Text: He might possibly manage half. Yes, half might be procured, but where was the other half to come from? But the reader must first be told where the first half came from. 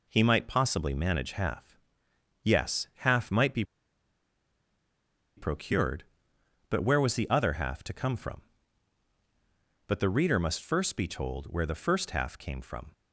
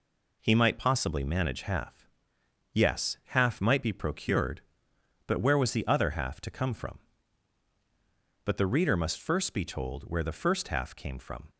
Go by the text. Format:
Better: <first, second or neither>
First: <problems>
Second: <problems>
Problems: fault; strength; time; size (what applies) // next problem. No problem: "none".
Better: second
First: pauses between "be" and "procured"; strong; at 3.6 s; 1.7 s long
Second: none